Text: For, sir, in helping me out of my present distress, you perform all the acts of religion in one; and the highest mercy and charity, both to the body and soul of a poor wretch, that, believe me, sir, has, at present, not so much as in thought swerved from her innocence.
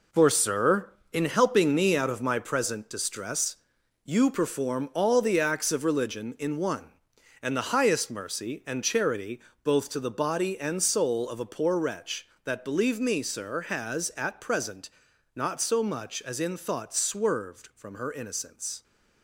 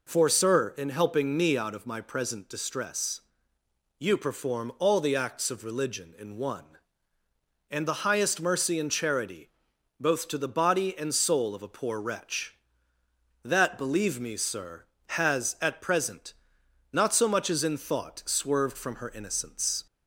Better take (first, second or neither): second